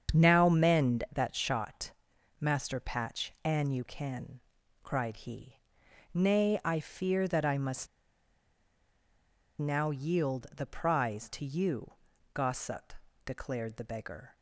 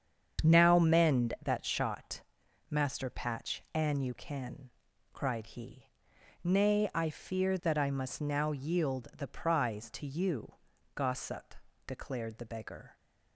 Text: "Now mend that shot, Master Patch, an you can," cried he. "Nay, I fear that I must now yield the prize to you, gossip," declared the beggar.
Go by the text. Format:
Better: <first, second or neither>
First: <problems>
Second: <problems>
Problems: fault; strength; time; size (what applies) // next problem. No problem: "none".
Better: second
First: starts louder than the rest; strong; until 1.2 s; 7.5 dB // pauses between "must" and "now"; strong; at 7.8 s; 1.7 s long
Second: starts louder than the rest; strong; until 1.5 s; 7.5 dB